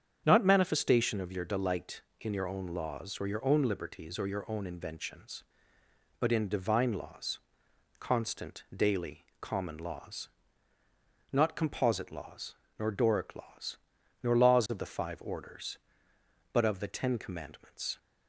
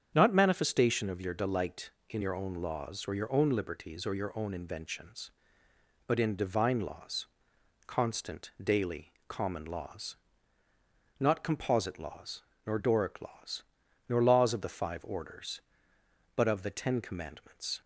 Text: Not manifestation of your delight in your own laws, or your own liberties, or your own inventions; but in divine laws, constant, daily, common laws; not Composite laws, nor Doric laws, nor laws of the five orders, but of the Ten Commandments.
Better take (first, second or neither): neither